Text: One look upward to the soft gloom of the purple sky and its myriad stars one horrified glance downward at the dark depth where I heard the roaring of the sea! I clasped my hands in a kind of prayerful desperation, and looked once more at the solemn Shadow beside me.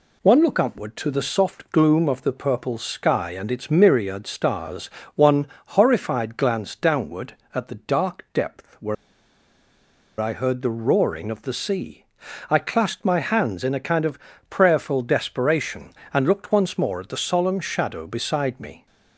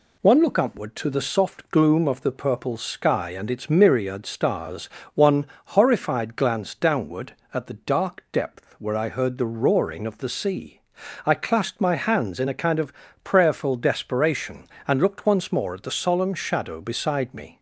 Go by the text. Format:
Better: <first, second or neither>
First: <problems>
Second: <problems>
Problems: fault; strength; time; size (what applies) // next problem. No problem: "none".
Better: second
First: pauses between "stars" and "one"; slight; at 4.8 s; 0.26 s long // pauses between "one" and "horrified"; slight; at 5.4 s; 0.20 s long // pauses between "where" and "I"; strong; at 8.9 s; 1.2 s long // pauses between "of" and "prayerful"; slight; at 14.1 s; 0.30 s long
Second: pauses between "stars" and "one"; slight; at 4.8 s; 0.26 s long // pauses between "one" and "horrified"; slight; at 5.4 s; 0.20 s long // pauses between "of" and "prayerful"; slight; at 12.9 s; 0.30 s long